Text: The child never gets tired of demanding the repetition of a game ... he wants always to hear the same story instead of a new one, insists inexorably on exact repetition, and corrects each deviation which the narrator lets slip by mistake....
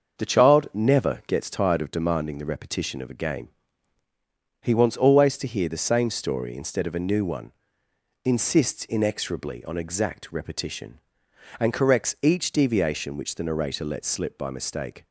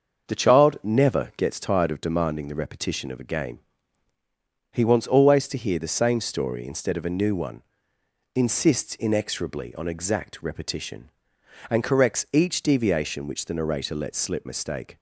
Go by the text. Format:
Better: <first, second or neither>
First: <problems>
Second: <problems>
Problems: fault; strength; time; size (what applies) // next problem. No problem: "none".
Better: first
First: starts louder than the rest; until 1.2 s; 6.5 dB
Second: starts louder than the rest; until 1.3 s; 6.5 dB // skips "by"; at 14.4 s